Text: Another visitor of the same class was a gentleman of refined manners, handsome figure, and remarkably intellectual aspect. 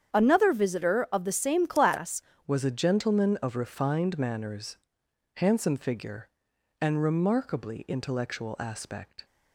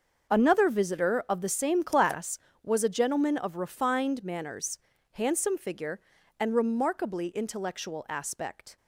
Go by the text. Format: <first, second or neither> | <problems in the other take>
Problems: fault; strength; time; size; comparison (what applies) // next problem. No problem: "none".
second | starts louder than the rest; strong; until 1.1 s; 8.5 dB; also in the second // changes voice at "was"; from 2.4 s on; 6.8 s long